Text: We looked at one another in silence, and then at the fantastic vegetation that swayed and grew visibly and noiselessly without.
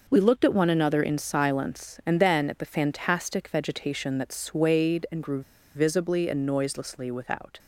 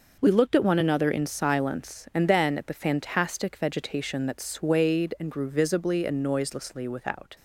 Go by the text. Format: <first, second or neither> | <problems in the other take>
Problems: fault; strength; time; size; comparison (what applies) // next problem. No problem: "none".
second | pauses between "grew" and "visibly"; slight; at 5.4 s; 0.33 s long